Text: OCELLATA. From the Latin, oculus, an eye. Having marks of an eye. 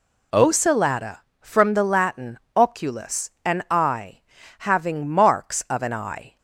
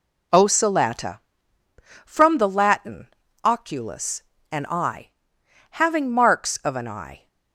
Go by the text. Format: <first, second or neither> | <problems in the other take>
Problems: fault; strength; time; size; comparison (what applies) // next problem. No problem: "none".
neither | none